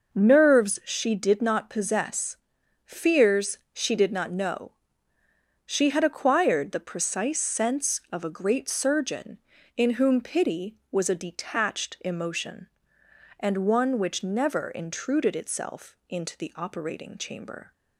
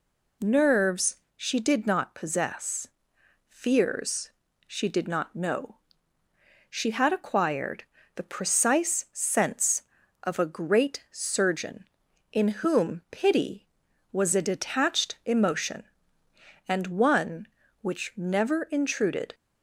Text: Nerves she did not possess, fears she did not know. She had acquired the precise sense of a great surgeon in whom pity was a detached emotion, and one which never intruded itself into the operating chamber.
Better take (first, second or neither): first